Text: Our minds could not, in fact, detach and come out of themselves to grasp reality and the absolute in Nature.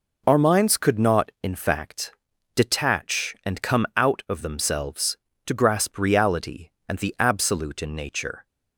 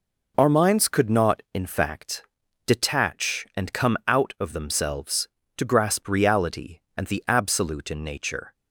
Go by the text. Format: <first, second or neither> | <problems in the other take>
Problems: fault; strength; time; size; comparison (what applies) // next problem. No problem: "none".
neither | none